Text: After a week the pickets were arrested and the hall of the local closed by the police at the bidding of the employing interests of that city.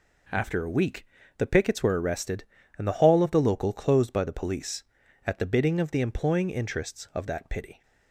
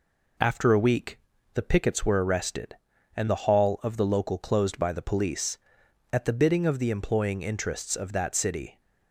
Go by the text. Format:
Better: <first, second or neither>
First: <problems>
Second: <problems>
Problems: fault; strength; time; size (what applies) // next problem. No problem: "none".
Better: second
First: pauses between "week" and "the"; slight; at 1.0 s; 0.33 s long // says "pity" for "city"; at 7.4 s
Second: pauses between "week" and "the"; slight; at 1.1 s; 0.36 s long